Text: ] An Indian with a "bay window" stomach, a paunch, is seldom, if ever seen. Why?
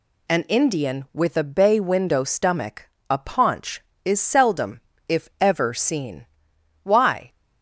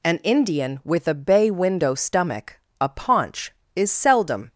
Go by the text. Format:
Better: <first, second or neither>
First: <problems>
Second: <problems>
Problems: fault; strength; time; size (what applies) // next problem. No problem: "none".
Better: first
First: none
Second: stops before "if ever seen Why"; at 4.5 s